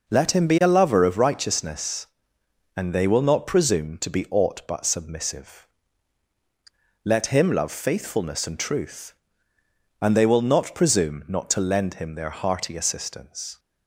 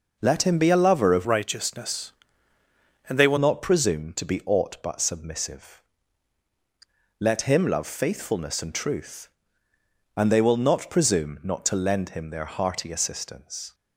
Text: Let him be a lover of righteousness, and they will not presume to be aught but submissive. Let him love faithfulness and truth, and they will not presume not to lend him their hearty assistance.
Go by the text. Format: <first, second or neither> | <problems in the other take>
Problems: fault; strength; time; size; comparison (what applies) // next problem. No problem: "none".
first | changes voice from "righteousness" to "will"; from 1.2 to 3.3 s; 2.1 s long